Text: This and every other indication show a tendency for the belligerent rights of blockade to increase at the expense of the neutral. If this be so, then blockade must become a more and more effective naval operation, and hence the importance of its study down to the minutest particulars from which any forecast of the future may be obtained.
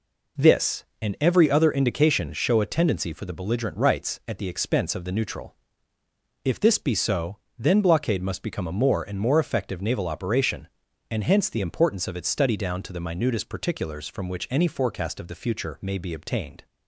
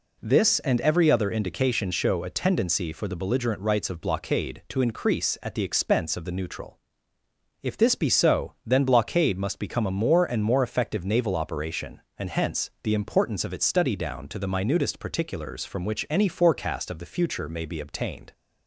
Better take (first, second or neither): second